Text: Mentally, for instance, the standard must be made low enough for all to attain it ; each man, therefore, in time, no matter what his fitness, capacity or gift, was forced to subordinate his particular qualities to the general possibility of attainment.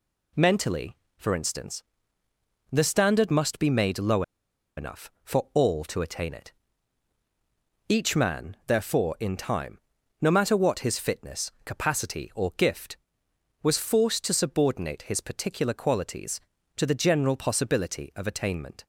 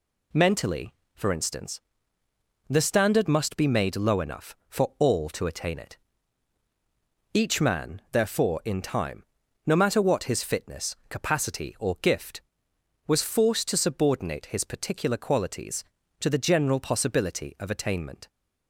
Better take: second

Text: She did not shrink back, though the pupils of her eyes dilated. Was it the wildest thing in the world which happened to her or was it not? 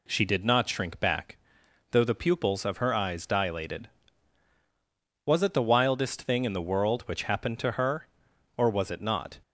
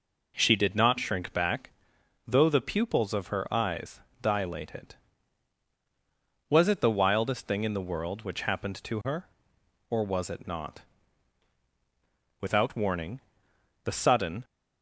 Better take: first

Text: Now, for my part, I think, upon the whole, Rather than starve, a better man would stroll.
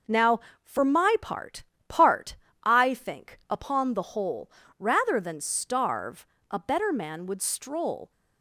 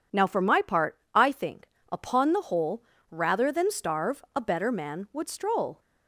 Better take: second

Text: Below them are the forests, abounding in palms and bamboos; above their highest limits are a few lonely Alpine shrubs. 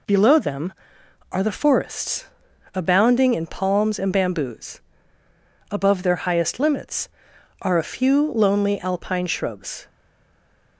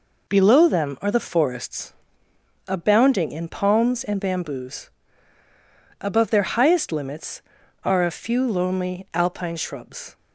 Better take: second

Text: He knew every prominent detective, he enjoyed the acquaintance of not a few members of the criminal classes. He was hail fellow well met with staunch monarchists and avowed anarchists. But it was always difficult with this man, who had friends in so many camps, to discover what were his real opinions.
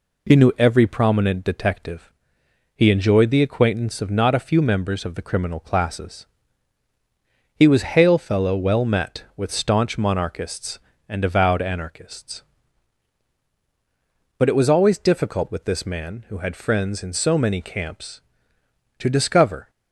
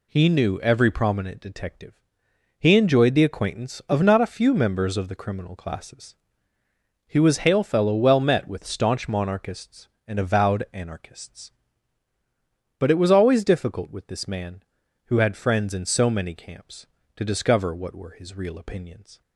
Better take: second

